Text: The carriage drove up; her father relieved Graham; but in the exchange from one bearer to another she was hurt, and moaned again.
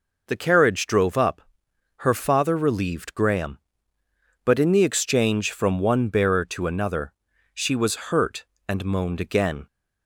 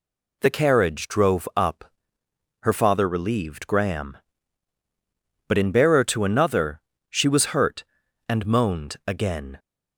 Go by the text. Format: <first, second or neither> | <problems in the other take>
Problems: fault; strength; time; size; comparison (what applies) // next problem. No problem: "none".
first | skips "the exchange from one"; at 5.7 s // pauses between "another" and "she"; slight; at 6.7 s; 0.30 s long; also in the first